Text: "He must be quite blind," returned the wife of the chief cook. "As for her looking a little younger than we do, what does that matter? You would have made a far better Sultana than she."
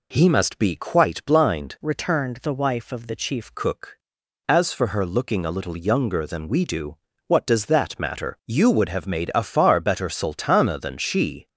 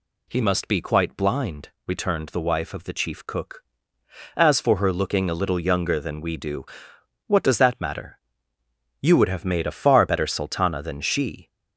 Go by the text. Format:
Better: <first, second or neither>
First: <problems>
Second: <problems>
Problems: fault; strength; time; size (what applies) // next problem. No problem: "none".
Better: second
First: changes voice from "returned" to "chief"; from 1.8 to 3.5 s; 1.7 s long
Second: none